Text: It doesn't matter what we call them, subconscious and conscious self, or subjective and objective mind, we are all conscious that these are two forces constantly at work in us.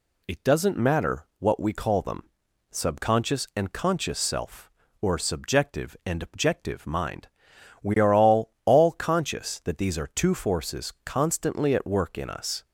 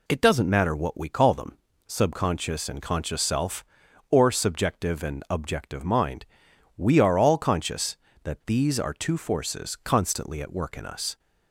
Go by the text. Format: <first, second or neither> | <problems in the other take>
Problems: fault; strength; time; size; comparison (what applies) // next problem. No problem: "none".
second | says "all" twice; at 8.6 s